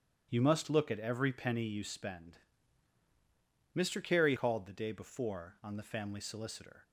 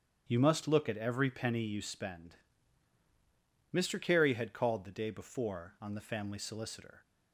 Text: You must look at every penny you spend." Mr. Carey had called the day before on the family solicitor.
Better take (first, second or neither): second